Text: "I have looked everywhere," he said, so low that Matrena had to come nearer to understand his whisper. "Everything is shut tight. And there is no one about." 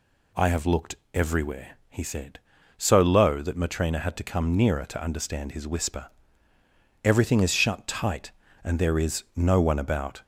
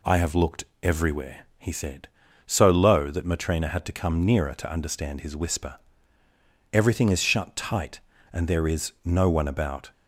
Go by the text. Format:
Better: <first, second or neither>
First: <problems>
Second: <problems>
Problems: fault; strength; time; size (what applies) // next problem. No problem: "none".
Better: second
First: gets louder; slight; throughout; 2 dB // pauses between "looked" and "everywhere"; slight; at 0.9 s; 0.18 s long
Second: pauses between "looked" and "everywhere"; slight; at 0.6 s; 0.18 s long